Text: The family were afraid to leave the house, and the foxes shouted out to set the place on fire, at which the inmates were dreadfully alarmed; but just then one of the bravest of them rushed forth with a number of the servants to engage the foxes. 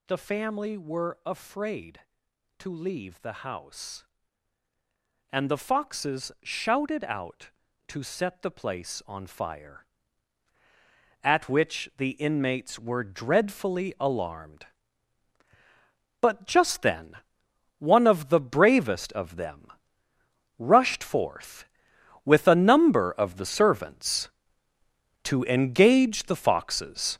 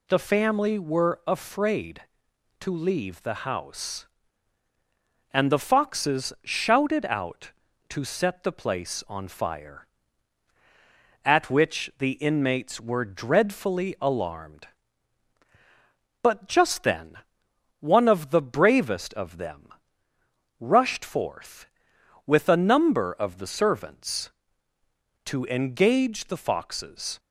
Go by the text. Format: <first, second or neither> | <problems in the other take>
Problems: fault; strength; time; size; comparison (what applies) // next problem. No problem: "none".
second | gets louder; strong; throughout; 8 dB // pauses between "then" and "one"; noticeable; at 17.1 s; 0.64 s long; noticeable in the second // pauses between "them" and "rushed"; noticeable; at 19.7 s; 0.88 s long; noticeable in the second